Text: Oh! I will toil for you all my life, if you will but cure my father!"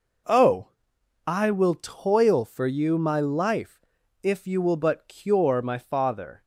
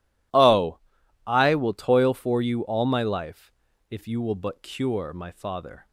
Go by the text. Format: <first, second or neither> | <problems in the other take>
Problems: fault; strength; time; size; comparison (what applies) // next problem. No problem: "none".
second | skips "all"; at 2.9 s